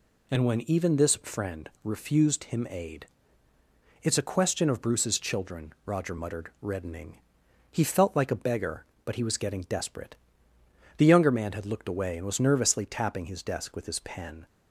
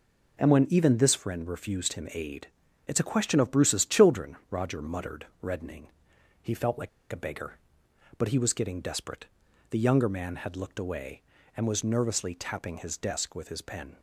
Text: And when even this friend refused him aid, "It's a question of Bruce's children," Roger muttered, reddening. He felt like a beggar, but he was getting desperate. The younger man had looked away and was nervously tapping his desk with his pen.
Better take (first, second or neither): first